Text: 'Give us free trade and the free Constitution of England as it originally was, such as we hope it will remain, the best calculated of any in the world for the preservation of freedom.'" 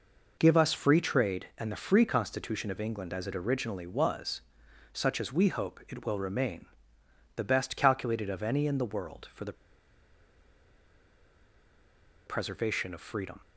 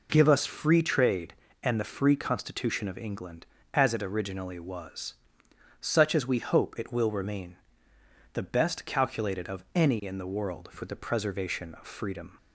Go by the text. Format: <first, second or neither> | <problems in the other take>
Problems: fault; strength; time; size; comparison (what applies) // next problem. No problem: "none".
second | pauses between "the" and "preservation"; strong; at 9.5 s; 2.7 s long